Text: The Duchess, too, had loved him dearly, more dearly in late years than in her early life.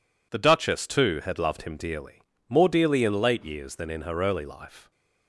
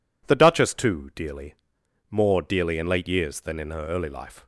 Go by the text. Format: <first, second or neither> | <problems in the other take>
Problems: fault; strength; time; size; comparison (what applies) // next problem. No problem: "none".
first | skips "had loved him"; at 1.1 s